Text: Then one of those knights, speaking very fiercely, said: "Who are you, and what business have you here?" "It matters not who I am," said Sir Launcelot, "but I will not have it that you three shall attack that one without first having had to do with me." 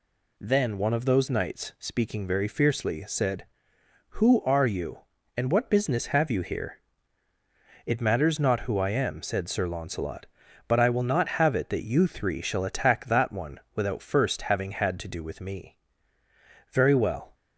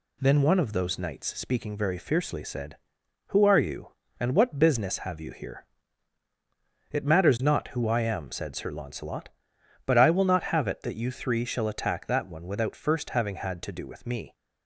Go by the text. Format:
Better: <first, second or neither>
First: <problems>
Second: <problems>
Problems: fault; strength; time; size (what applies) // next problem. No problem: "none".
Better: second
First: pauses between "one" and "without"; slight; at 13.5 s; 0.16 s long // goes on to say "Very well"; noticeable; from 16.6 s on; 0.64 s long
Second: none